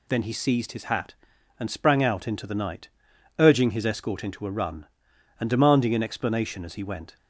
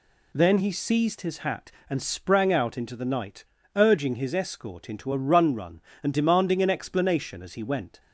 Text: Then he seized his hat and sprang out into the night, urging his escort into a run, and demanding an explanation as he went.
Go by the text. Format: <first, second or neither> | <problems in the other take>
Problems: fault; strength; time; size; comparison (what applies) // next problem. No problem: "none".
first | says "run" twice; at 5.5 s